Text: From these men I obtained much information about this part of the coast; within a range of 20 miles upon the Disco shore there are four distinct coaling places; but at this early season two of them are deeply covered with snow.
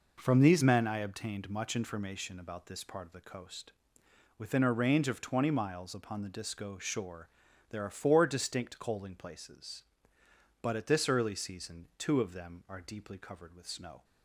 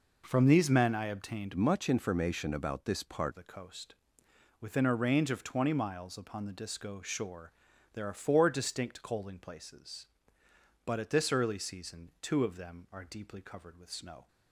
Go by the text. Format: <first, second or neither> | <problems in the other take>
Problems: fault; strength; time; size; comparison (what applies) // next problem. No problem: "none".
first | changes voice from "much" to "part"; from 1.5 to 3.3 s; 1.8 s long // pauses between "shore" and "there"; at 7.5 s; 0.40 s long; also in the first